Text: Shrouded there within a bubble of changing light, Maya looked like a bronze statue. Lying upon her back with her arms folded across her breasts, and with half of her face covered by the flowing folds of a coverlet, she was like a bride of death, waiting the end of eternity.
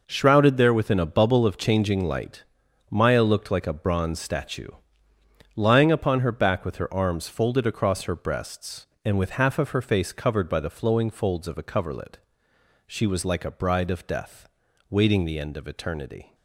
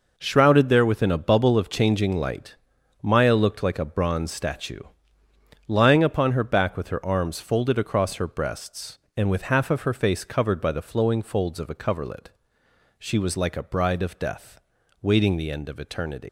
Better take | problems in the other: first | leaves "eternity" unfinished; at 16.2 s; 175 ms

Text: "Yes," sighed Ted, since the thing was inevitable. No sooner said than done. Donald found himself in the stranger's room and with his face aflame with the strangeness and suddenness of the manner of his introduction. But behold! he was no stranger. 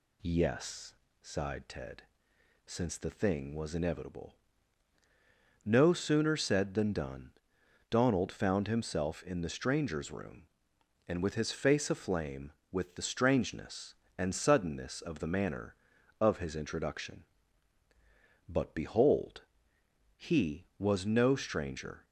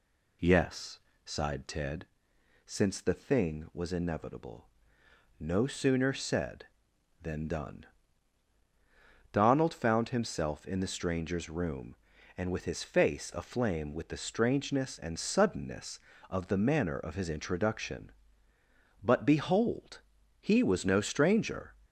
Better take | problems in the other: neither | none

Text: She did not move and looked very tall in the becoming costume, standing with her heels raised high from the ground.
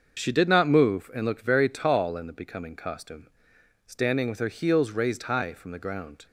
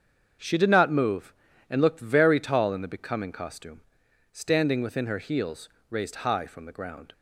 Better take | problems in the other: first | starts louder than the rest; strong; until 1.7 s; 7 dB; also in the first // says "within" for "with"; at 4.7 s // pauses between "heels" and "raised"; slight; at 5.6 s; 0.22 s long

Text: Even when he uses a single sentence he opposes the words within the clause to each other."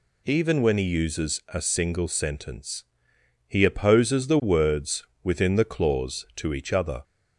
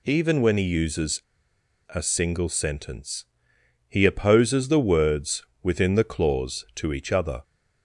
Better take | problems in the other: first | pauses between "uses" and "a"; noticeable; at 1.2 s; 0.69 s long // pauses between "sentence" and "he"; noticeable; at 3.2 s; 0.62 s long; noticeable in the first // pauses between "words" and "within"; slight; at 5.4 s; 0.18 s long; slight in the first

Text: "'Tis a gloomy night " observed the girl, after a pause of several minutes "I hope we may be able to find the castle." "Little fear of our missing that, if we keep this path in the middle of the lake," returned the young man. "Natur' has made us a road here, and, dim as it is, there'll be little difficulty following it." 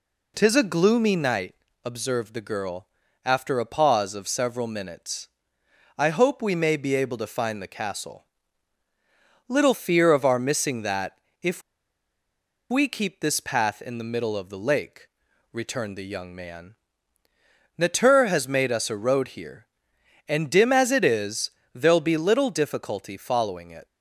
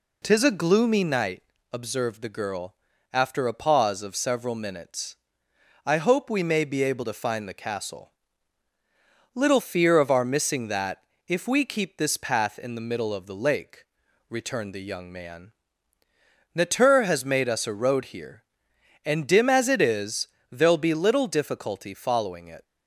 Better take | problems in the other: second | pauses between "minutes" and "I"; noticeable; at 5.2 s; 0.68 s long; noticeable in the second // pauses between "if" and "we"; at 11.6 s; 1.0 s long

